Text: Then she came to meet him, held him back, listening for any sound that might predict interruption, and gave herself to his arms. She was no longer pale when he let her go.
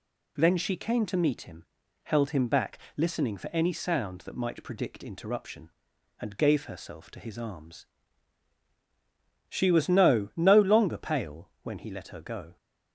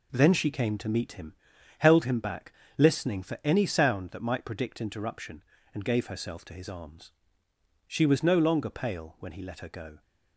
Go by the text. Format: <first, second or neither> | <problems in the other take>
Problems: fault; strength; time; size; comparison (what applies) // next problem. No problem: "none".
second | says "no" twice; at 10.3 s